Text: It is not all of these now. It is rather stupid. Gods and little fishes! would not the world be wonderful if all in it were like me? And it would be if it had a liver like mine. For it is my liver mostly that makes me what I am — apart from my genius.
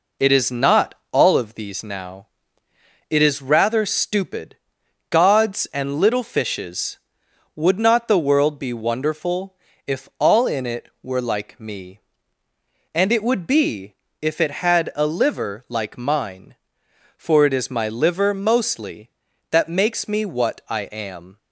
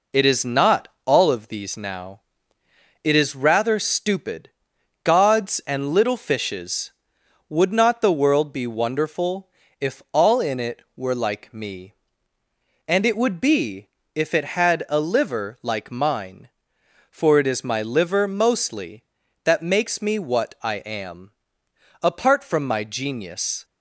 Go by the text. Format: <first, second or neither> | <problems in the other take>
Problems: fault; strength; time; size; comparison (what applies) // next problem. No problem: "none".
second | pauses between "not" and "all"; slight; at 0.9 s; 0.16 s long; slight in the second // pauses between "wonderful" and "if"; slight; at 9.5 s; 0.32 s long; slight in the second // pauses between "be" and "if"; slight; at 13.9 s; 0.28 s long; slight in the second // stops before "apart from my genius"; at 21.3 s